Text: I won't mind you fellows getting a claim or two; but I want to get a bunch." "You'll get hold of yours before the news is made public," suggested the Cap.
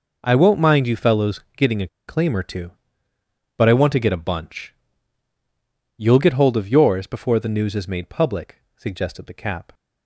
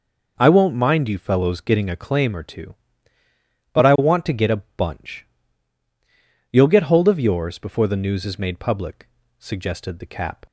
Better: second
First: pauses between "fellows" and "getting"; slight; at 1.4 s; 0.16 s long // pauses between "a" and "claim"; slight; at 1.8 s; 0.20 s long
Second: none

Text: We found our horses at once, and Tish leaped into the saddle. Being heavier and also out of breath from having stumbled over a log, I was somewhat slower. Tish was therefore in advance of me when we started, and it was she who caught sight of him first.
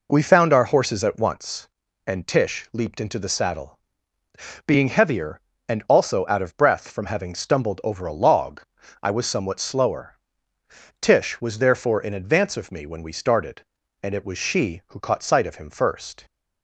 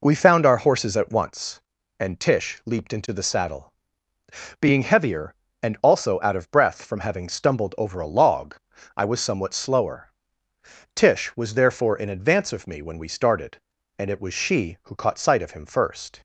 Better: neither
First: none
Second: none

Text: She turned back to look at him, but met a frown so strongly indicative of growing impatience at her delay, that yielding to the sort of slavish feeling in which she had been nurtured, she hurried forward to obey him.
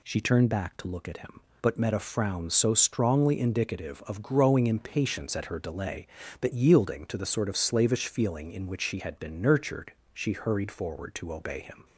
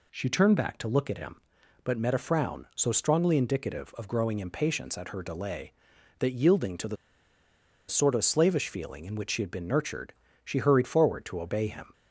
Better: first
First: none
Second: pauses between "the" and "sort"; noticeable; at 6.9 s; 0.94 s long

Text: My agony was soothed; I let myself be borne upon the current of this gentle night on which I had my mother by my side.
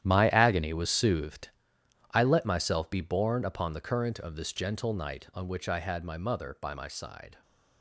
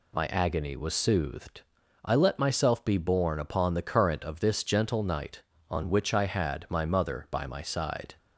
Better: second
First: gets quieter; strong; throughout; 12 dB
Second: none

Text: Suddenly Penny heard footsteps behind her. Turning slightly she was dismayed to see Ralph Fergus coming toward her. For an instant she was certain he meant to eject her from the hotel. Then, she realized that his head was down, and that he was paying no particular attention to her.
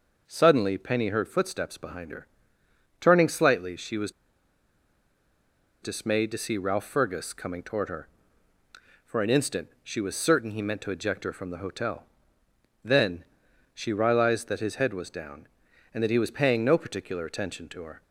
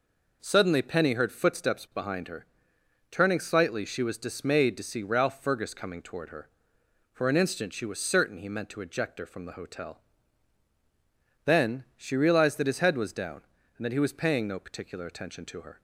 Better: second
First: pauses between "was" and "dismayed"; strong; at 4.1 s; 1.7 s long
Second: none

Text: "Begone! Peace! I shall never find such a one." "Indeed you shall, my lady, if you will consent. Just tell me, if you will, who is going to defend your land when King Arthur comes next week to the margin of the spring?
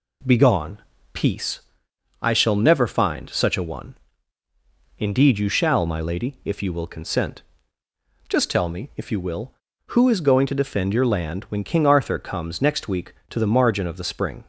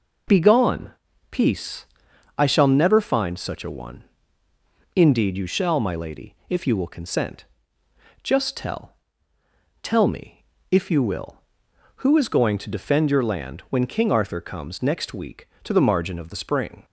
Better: first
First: none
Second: says "tell" twice; at 9.8 s

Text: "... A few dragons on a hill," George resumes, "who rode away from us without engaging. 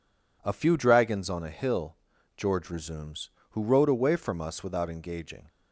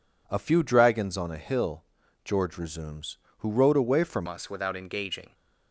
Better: first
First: none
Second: changes voice at "us"; from 4.2 s on; 1.1 s long

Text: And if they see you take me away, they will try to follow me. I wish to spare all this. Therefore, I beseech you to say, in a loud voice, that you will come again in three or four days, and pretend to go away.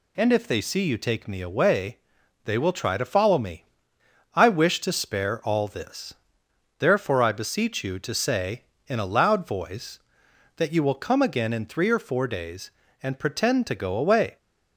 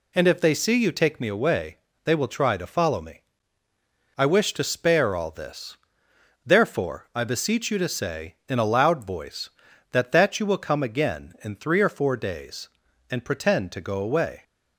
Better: first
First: none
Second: says "that" twice; at 10.1 s

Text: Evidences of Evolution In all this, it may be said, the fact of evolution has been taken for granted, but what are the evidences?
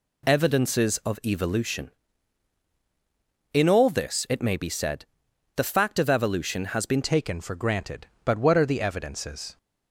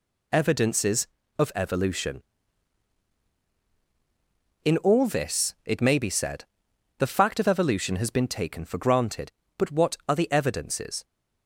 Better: second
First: changes voice at "taken"; from 7.0 s on; 2.5 s long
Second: none

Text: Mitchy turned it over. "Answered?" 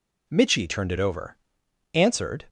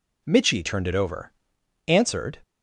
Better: neither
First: none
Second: none

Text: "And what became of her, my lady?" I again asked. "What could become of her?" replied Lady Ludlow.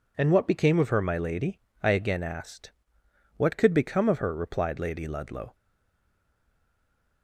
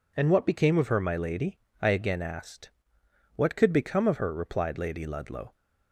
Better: second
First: stays silent after the last word; noticeable; from 5.5 s on; 1.7 s long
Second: none

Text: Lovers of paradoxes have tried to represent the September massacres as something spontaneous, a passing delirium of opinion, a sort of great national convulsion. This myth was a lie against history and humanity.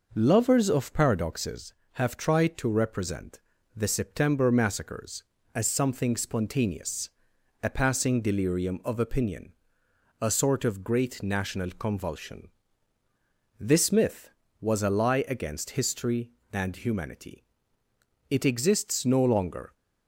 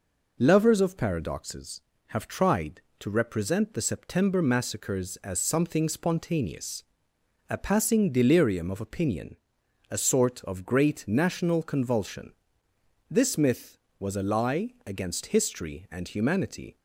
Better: second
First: pauses between "represent" and "the"; at 3.3 s; 0.38 s long // goes on to say "It exists no longer"; from 18.3 s on; 1.4 s long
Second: none

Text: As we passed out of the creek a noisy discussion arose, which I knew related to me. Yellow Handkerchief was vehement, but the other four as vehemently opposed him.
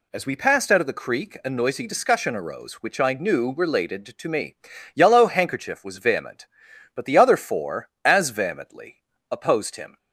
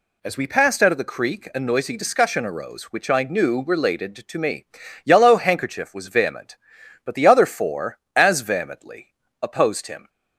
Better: neither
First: pauses between "vehemently" and "opposed"; slight; at 9.0 s; 0.28 s long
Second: pauses between "vehemently" and "opposed"; slight; at 9.1 s; 0.28 s long

